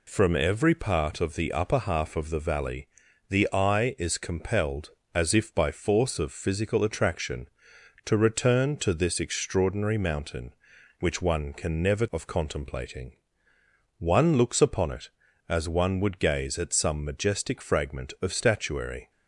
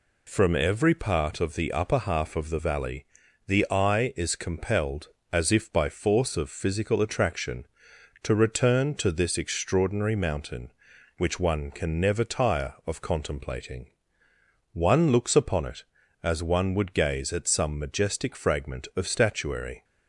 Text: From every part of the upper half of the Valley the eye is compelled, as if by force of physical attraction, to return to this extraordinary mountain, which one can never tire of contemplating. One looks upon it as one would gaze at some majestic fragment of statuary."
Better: second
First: pauses between "Valley" and "the"; at 2.8 s; 0.40 s long // skips "tire"; at 12.0 s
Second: pauses between "Valley" and "the"; at 3.0 s; 0.40 s long

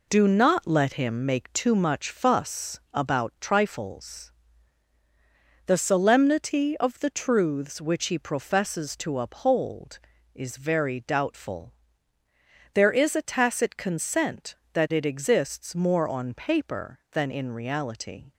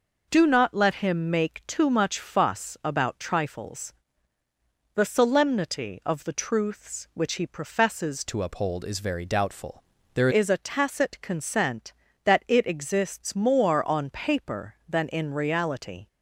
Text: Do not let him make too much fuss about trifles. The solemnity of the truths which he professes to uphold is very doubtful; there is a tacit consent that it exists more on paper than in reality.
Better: first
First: none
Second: changes voice from "to" to "there"; from 8.2 to 10.2 s; 2.0 s long

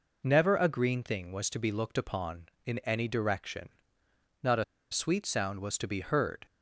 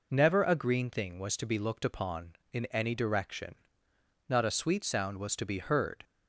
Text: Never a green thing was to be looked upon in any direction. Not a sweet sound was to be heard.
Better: second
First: pauses between "a" and "sweet"; slight; at 4.6 s; 0.27 s long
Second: none

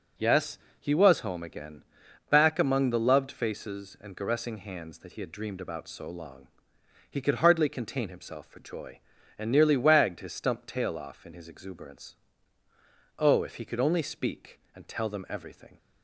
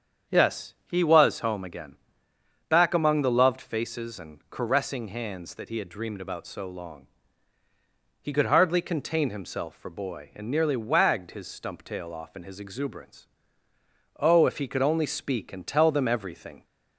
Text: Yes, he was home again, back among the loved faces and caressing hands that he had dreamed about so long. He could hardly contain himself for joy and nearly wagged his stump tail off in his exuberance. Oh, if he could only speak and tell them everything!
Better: first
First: none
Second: starts louder than the rest; strong; until 1.4 s; 8 dB // says "boy" for "joy"; at 9.8 s

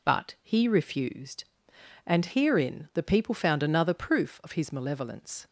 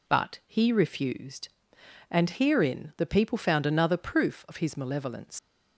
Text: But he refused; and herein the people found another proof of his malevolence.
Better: first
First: none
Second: leaves "malevolence" unfinished; at 5.3 s; 120 ms

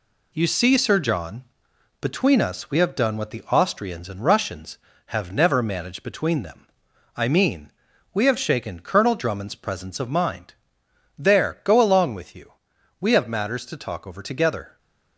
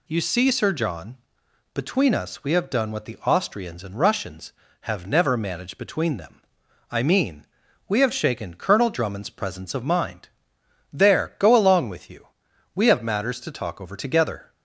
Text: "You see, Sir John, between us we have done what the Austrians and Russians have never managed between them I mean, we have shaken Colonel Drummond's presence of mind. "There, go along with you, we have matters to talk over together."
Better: second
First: gets quieter; noticeable; throughout; 5.5 dB // pauses between "them" and "I"; noticeable; at 6.6 s; 0.52 s long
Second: pauses between "them" and "I"; noticeable; at 6.4 s; 0.52 s long

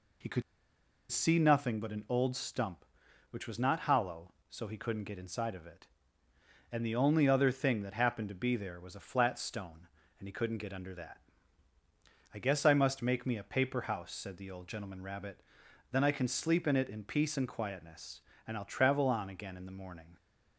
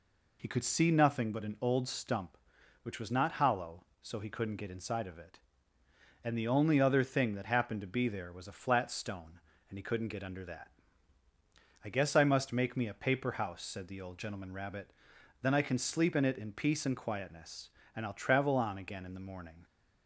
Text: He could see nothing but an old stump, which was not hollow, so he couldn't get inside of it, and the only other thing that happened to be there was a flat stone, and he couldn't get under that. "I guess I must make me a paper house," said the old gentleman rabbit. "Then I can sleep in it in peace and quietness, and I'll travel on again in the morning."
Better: second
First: pauses between "could" and "see"; noticeable; at 0.4 s; 0.69 s long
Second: none

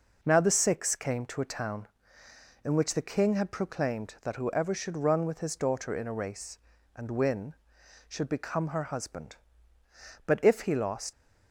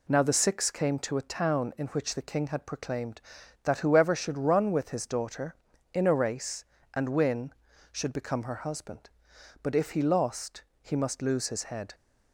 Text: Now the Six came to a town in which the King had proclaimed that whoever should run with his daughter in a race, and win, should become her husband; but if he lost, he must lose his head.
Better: second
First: stops before "he must lose his head"; at 11.1 s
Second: none

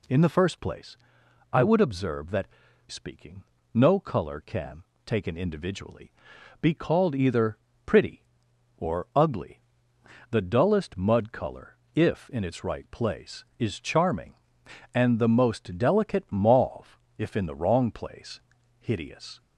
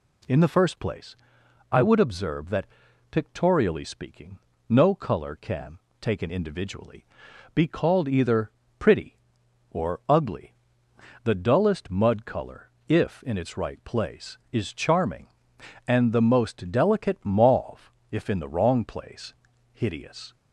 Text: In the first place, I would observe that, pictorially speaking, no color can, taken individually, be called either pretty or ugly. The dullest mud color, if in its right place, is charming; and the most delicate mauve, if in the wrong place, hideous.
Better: second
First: skips "pictorially"; at 2.6 s // pauses between "either" and "pretty"; slight; at 7.5 s; 0.26 s long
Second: pauses between "either" and "pretty"; slight; at 8.5 s; 0.26 s long

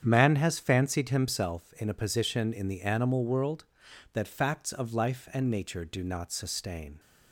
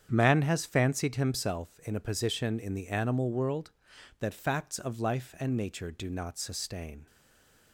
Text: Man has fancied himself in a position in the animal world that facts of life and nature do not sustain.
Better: first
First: starts louder than the rest; strong; until 1.0 s; 8 dB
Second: starts louder than the rest; strong; until 1.1 s; 8 dB // stays silent after the last word; slight; from 7.0 s on; 0.7 s long

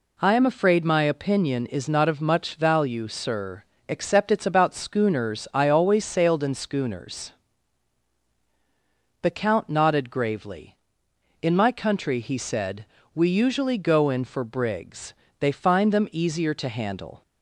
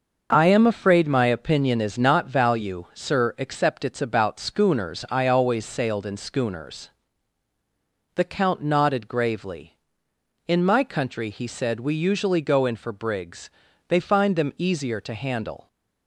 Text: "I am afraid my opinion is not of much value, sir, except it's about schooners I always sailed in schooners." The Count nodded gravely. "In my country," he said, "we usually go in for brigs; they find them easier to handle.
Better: first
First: none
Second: starts louder than the rest; until 1.3 s; 6.5 dB // skips "of much"; at 2.2 s

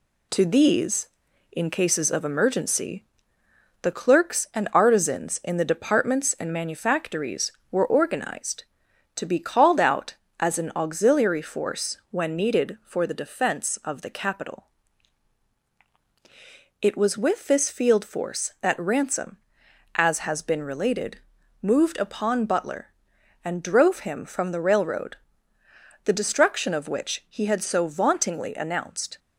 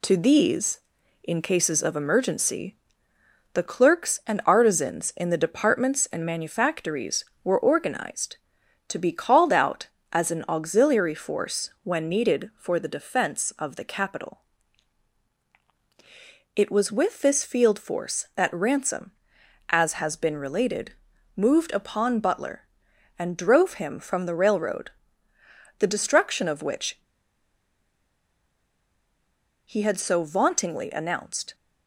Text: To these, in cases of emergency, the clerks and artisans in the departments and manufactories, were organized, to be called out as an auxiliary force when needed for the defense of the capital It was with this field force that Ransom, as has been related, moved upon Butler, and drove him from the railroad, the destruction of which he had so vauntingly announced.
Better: first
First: pauses between "capital" and "It"; strong; at 14.6 s; 2.1 s long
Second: pauses between "capital" and "It"; strong; at 14.4 s; 2.1 s long // pauses between "which" and "he"; strong; at 26.9 s; 2.6 s long

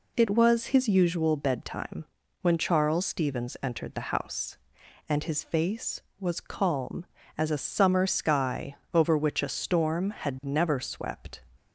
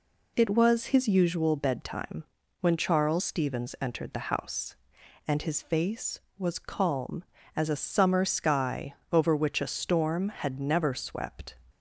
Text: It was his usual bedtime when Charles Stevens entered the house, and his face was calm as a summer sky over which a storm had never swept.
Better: neither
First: pauses between "bedtime" and "when"; at 2.0 s; 0.38 s long // pauses between "sky" and "over"; slight; at 8.7 s; 0.16 s long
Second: pauses between "bedtime" and "when"; at 2.2 s; 0.38 s long // pauses between "sky" and "over"; slight; at 8.9 s; 0.16 s long

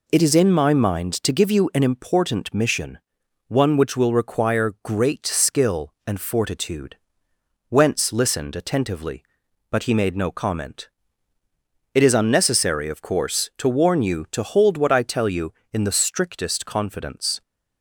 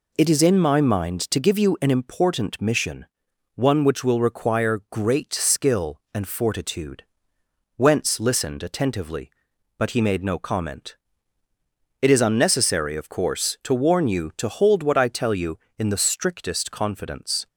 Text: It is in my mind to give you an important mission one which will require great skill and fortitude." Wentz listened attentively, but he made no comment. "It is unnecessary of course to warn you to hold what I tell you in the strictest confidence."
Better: neither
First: pauses between "mission" and "one"; noticeable; at 2.9 s; 0.48 s long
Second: pauses between "mission" and "one"; noticeable; at 3.0 s; 0.48 s long

